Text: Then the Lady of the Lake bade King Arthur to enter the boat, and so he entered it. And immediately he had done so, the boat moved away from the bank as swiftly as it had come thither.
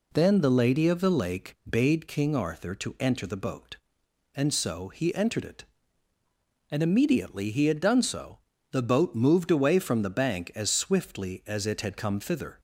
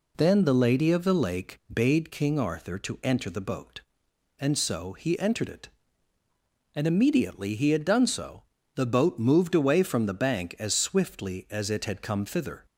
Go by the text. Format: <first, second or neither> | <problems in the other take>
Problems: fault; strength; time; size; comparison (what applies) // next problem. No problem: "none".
neither | none